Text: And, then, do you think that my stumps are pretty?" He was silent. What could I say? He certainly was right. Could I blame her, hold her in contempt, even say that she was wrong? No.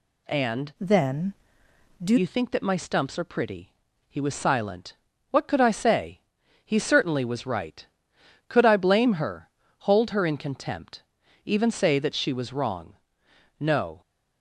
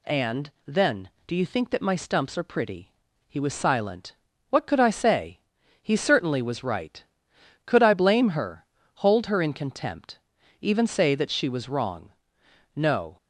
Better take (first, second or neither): second